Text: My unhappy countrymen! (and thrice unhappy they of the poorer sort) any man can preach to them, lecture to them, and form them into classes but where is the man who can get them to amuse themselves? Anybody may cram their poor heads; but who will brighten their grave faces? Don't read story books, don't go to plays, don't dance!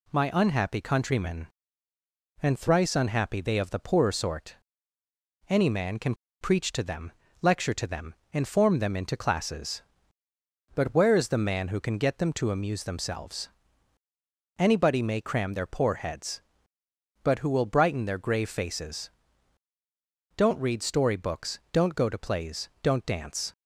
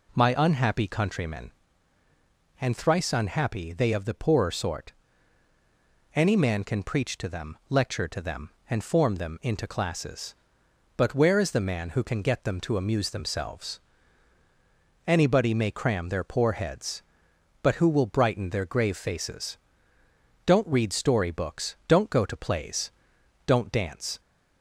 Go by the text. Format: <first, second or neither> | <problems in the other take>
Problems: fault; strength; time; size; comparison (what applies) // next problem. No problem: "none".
second | pauses between "can" and "preach"; slight; at 6.1 s; 0.25 s long